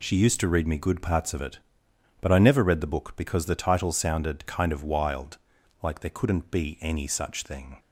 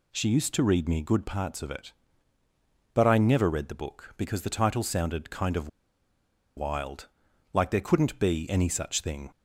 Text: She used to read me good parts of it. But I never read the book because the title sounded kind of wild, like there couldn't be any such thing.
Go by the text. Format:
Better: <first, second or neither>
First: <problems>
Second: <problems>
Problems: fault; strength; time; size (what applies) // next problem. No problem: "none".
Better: first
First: none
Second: pauses between "of" and "wild"; noticeable; at 5.6 s; 0.89 s long